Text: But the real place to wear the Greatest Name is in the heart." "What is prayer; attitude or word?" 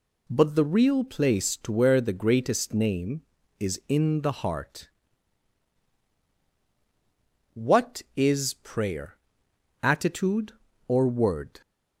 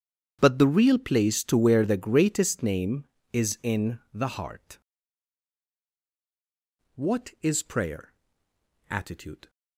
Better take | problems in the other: first | starts louder than the rest; strong; until 1.4 s; 8.5 dB // stops before "or word"; at 9.4 s

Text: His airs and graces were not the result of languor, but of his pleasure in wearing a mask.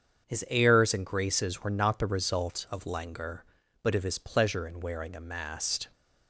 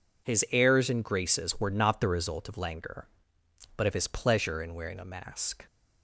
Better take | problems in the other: second | starts louder than the rest; until 1.3 s; 7 dB // says "mast" for "mask"; at 5.1 s

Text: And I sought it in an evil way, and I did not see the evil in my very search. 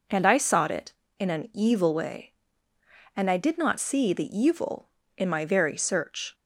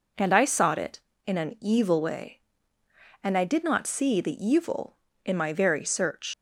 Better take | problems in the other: first | leaves "search" unfinished; at 6.3 s; 85 ms

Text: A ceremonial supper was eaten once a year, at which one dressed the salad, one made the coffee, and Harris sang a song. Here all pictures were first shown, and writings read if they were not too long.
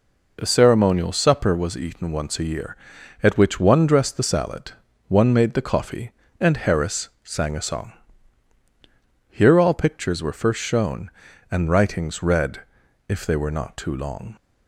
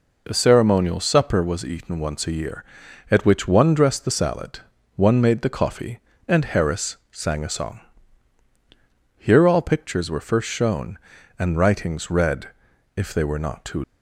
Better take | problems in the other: first | pauses between "read" and "if"; noticeable; at 12.4 s; 0.48 s long; noticeable in the first // stops before "long"; at 13.8 s

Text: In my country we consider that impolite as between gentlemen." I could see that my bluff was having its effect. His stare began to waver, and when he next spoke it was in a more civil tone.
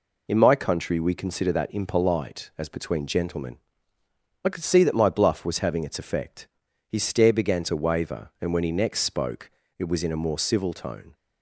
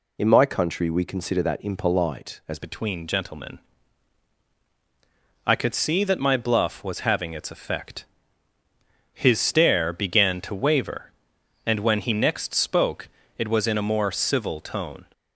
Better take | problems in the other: first | changes voice at "between"; from 2.5 s on; 12.5 s long // pauses between "spoke" and "it"; slight; at 13.0 s; 0.28 s long; slight in the first

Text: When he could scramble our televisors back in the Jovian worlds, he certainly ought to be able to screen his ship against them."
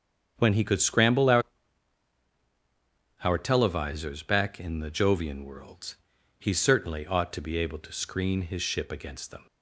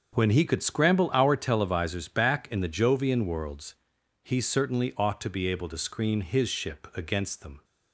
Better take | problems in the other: second | starts louder than the rest; strong; until 1.3 s; 8 dB; also in the second // says "our" twice; at 3.2 s

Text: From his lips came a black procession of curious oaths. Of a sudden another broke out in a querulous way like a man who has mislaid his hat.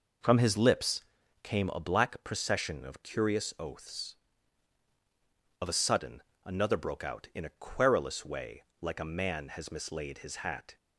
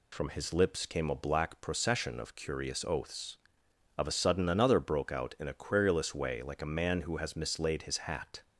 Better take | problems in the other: second | pauses between "lips" and "came"; at 1.0 s; 0.40 s long // pauses between "sudden" and "another"; slight; at 6.2 s; 0.22 s long // pauses between "way" and "like"; slight; at 8.6 s; 0.18 s long // skips "who"; at 9.4 s

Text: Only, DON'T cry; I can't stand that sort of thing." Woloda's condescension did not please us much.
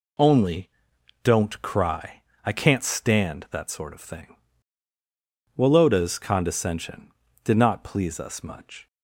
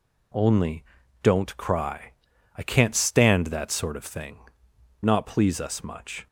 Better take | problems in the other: first | skips "Woloda's condescension did"; at 4.7 s

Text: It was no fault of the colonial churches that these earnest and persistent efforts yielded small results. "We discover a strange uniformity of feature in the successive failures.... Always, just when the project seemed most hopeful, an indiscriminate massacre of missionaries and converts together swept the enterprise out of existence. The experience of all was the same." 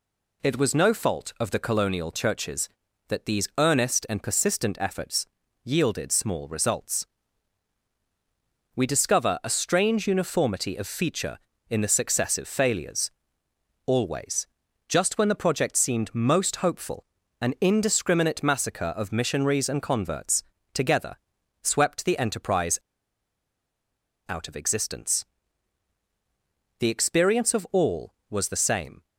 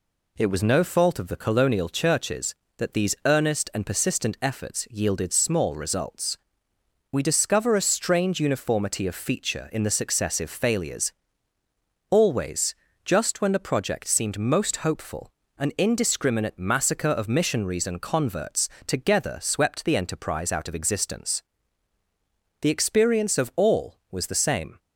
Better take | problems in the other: second | pauses between "efforts" and "yielded"; at 5.2 s; 0.38 s long // pauses between "converts" and "together"; slight; at 20.4 s; 0.30 s long; slight in the second // pauses between "together" and "swept"; noticeable; at 21.1 s; 0.48 s long // pauses between "enterprise" and "out"; strong; at 22.7 s; 1.5 s long

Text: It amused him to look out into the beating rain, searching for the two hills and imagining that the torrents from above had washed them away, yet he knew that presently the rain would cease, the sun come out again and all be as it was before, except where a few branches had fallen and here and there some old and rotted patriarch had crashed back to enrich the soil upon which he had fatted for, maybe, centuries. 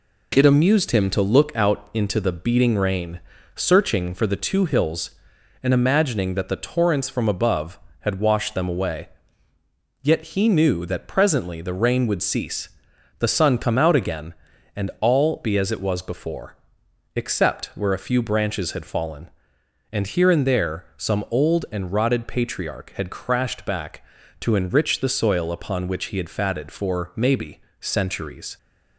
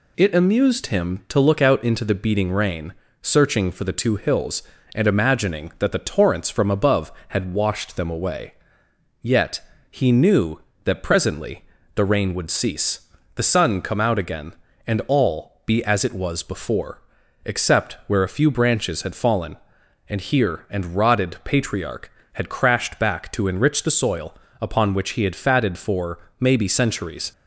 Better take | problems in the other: first | pauses between "yet" and "he"; slight; at 9.5 s; 0.30 s long // pauses between "presently" and "the"; slight; at 11.6 s; 0.32 s long // skips "there some old and"; at 20.9 s // pauses between "soil" and "upon"; slight; at 24.3 s; 0.28 s long

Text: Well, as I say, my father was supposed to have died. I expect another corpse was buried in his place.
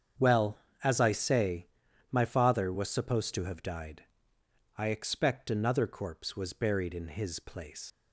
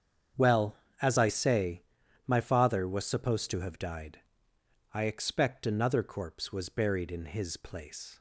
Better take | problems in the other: second | starts louder than the rest; strong; until 1.4 s; 7.5 dB; strong in the second // leaves "place" unfinished; at 7.9 s; 110 ms

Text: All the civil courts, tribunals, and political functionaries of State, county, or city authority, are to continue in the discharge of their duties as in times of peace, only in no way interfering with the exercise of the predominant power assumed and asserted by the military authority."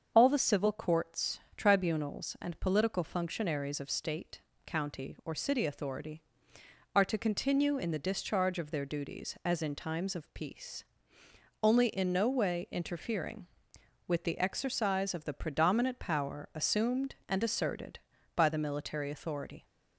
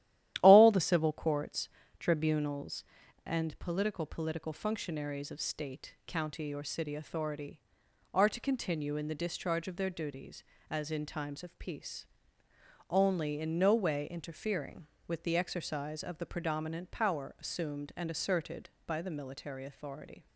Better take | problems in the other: first | starts louder than the rest; strong; until 1.4 s; 12.5 dB; also in the first // says "political" twice; at 4.0 s

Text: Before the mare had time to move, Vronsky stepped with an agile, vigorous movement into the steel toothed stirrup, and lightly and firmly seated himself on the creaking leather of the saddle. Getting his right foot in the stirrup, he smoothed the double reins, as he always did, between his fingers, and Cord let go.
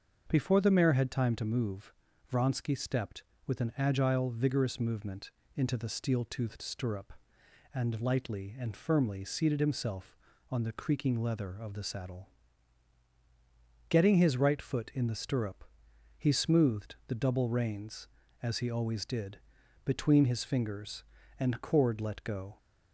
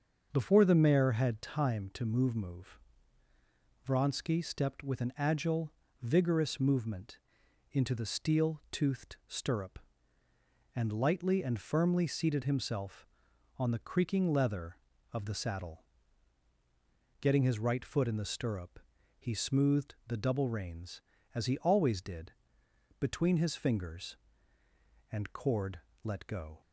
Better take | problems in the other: first | starts louder than the rest; until 1.3 s; 6.5 dB; also in the first // says "move" twice; at 2.3 s // pauses between "movement" and "into"; noticeable; at 7.1 s; 0.54 s long; slight in the first // pauses between "Cord" and "let"; slight; at 25.8 s; 0.24 s long

